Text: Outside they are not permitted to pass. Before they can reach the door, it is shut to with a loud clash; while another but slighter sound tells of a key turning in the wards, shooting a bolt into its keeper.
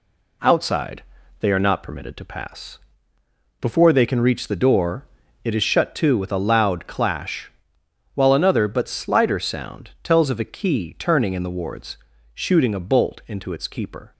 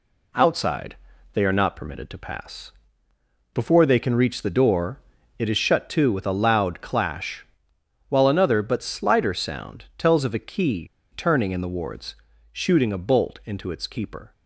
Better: first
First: pauses between "Outside" and "they"; slight; at 1.0 s; 0.36 s long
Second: pauses between "Outside" and "they"; slight; at 0.9 s; 0.36 s long // pauses between "key" and "turning"; slight; at 10.8 s; 0.28 s long

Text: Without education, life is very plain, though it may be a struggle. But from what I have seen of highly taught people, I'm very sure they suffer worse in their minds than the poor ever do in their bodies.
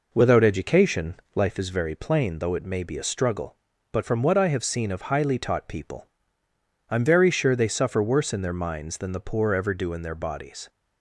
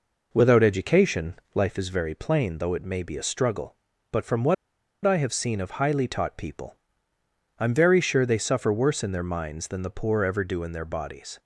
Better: first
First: none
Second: pauses between "what" and "I"; noticeable; at 4.5 s; 0.50 s long

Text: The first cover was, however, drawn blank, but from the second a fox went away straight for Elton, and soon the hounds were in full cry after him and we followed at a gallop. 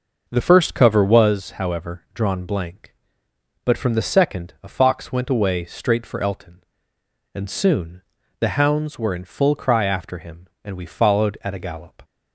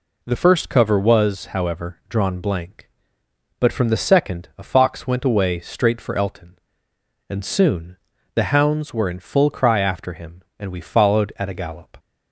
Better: second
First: starts louder than the rest; noticeable; until 1.4 s; 5.5 dB // pauses between "soon" and "the"; at 8.0 s; 0.40 s long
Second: pauses between "soon" and "the"; at 7.9 s; 0.40 s long

